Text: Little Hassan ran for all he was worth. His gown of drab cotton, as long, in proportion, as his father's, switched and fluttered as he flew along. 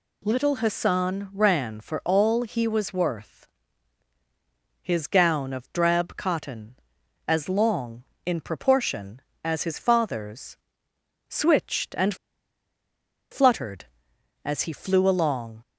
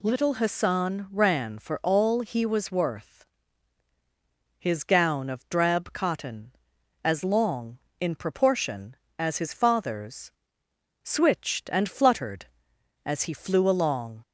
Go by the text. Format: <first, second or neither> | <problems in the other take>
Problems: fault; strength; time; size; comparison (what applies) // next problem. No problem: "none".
second | pauses between "and" and "fluttered"; at 12.1 s; 1.1 s long